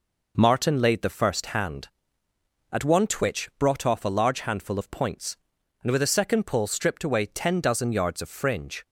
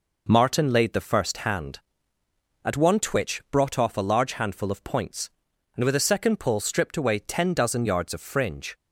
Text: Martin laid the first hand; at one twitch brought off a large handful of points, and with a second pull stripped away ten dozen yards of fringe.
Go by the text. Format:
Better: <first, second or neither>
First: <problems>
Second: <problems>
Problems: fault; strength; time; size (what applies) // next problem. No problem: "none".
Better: neither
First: none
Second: none